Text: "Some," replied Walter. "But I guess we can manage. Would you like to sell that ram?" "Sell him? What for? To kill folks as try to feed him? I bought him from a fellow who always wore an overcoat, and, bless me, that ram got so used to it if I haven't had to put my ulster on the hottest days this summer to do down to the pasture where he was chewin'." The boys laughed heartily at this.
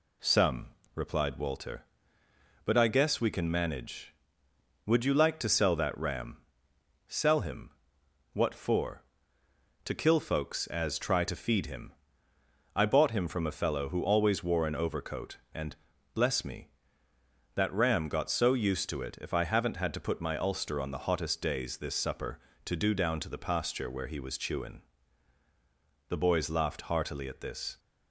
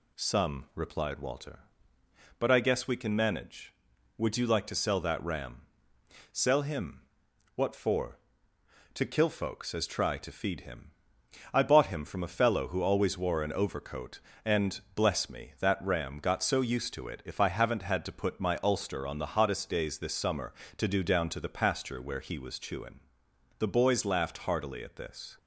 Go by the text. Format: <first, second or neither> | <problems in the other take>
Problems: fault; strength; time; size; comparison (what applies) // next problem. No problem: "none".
second | says "supper" for "summer"; at 21.9 s